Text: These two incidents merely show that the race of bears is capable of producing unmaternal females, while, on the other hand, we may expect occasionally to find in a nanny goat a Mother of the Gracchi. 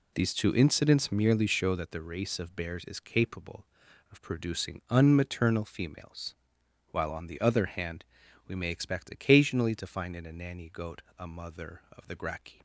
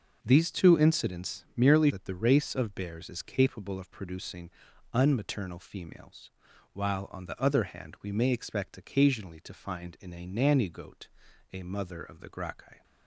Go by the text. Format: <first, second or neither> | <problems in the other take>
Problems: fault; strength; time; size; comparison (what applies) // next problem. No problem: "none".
first | skips "show"; at 1.8 s // pauses between "producing" and "unmaternal"; noticeable; at 4.4 s; 0.46 s long // pauses between "goat" and "a"; at 11.0 s; 0.42 s long; slight in the first